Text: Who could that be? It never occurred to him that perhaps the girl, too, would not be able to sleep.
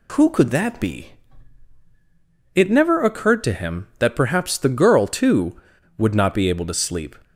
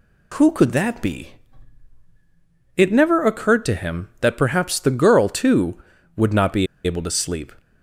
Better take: first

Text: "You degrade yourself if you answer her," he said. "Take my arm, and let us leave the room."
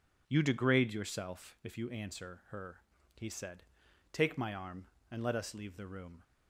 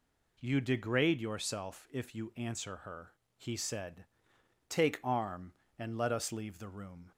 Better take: first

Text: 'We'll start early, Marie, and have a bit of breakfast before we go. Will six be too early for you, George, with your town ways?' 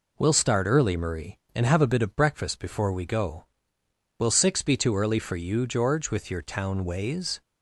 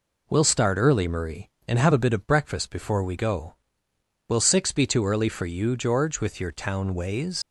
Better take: first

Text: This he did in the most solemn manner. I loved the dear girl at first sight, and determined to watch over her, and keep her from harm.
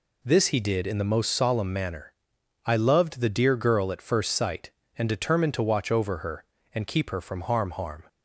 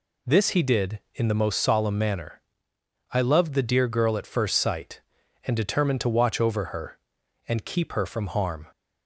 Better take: second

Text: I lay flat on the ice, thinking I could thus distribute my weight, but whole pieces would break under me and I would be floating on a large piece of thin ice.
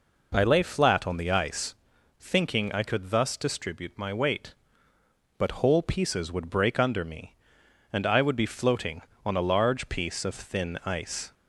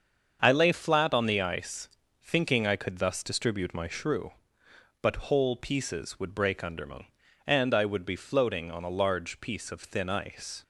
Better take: first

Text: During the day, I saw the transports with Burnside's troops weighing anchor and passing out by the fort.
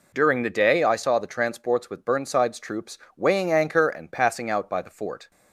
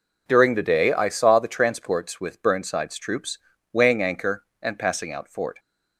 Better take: first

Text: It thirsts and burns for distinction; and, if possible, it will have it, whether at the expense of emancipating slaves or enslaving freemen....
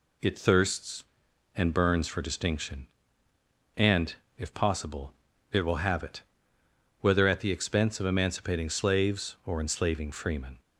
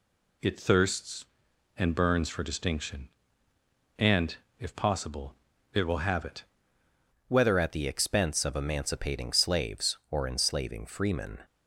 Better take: first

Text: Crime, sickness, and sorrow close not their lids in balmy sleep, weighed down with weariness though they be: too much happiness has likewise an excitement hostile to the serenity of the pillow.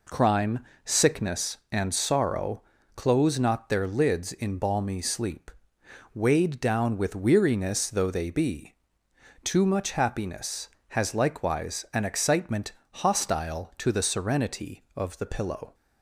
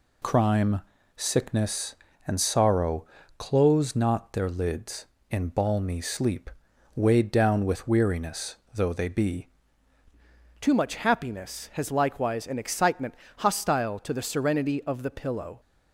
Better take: first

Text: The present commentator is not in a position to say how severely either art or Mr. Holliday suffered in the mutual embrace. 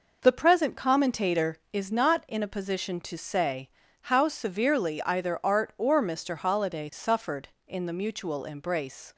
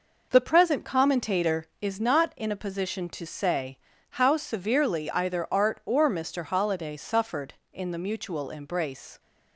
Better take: neither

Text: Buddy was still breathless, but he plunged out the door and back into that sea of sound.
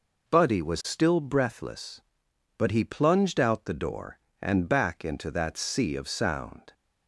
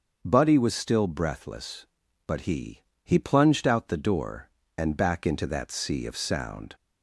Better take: first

